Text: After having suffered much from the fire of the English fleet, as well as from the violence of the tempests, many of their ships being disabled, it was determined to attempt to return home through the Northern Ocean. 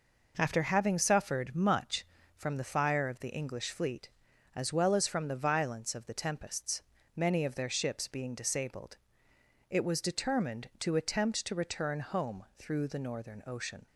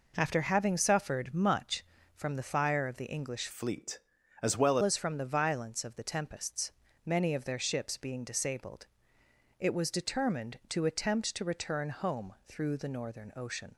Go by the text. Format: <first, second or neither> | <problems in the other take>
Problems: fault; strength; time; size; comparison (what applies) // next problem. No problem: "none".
first | changes voice from "fleet" to "well"; from 3.5 to 4.7 s; 1.2 s long